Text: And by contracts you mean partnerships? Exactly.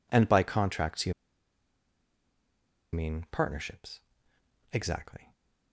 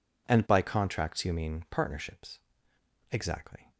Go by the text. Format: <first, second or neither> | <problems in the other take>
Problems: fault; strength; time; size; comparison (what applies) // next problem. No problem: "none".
second | pauses between "you" and "mean"; strong; at 1.1 s; 1.8 s long